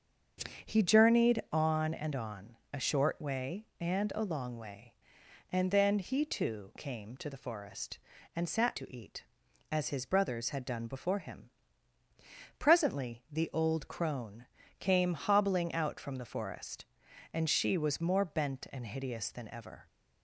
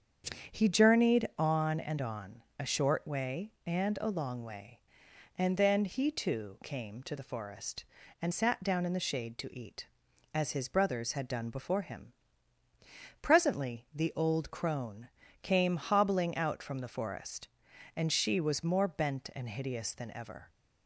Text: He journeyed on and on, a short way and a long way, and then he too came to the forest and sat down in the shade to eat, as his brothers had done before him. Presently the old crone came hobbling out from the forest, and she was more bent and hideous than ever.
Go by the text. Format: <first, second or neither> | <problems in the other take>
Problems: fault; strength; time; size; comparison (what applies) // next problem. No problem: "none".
second | starts louder than the rest; strong; until 1.7 s; 7 dB; strong in the second // skips "down in the shade"; at 8.7 s // pauses between "crone" and "came"; slight; at 14.4 s; 0.32 s long; slight in the second